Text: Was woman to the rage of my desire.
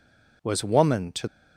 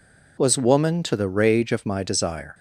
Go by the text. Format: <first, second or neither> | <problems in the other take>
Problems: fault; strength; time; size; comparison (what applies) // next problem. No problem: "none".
second | stops before "the rage of my desire"; at 1.2 s